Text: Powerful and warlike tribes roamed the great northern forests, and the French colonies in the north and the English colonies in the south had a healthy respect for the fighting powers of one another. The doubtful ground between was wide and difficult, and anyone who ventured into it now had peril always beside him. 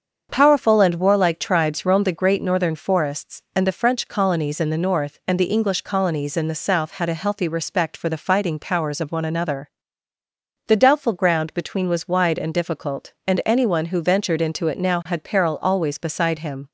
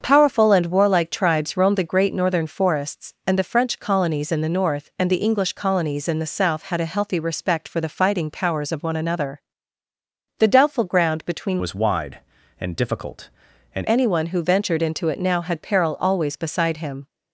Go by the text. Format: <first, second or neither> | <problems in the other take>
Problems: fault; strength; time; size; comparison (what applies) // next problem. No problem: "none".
first | starts louder than the rest; until 1.0 s; 7 dB; also in the first // changes voice from "was" to "and"; from 11.5 to 13.8 s; 2.3 s long